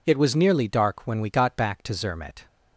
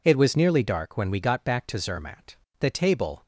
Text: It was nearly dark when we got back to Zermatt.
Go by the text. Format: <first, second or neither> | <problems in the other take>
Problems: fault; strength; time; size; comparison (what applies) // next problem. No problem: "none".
first | goes on to say "The table"; noticeable; from 2.6 s on; 0.62 s long